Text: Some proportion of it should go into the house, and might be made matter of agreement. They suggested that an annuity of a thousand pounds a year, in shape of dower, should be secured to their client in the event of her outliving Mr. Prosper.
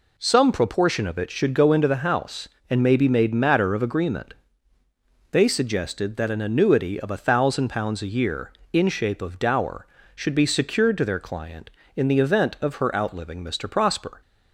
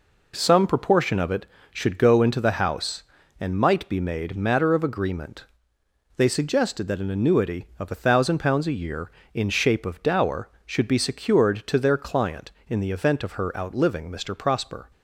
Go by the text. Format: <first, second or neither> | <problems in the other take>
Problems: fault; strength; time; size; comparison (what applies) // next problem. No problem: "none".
second | says "may" for "might"; at 2.8 s